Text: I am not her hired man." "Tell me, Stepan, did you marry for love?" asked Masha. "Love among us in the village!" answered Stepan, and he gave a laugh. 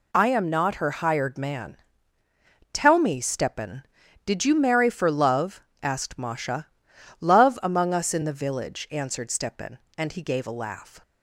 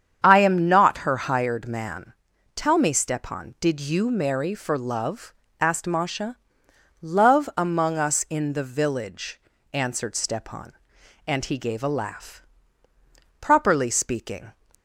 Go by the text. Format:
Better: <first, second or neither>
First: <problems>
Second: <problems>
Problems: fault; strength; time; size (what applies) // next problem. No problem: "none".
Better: first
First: none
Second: starts louder than the rest; strong; until 1.2 s; 8 dB // goes on to say "Properly speaking"; noticeable; from 13.3 s on; 1.1 s long